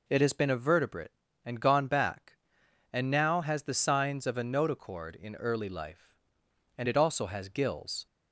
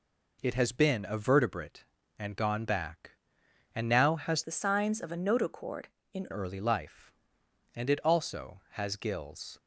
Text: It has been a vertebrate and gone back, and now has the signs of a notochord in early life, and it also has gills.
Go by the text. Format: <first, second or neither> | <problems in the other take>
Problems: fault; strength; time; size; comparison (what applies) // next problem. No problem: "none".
first | changes voice from "the" to "in"; from 4.4 to 6.2 s; 1.8 s long